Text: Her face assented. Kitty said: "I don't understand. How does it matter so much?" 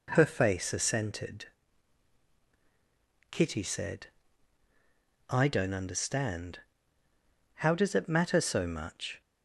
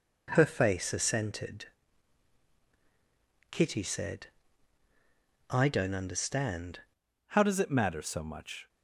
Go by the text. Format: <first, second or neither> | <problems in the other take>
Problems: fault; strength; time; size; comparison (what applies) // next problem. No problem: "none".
first | changes voice at "How"; from 7.2 s on; 1.4 s long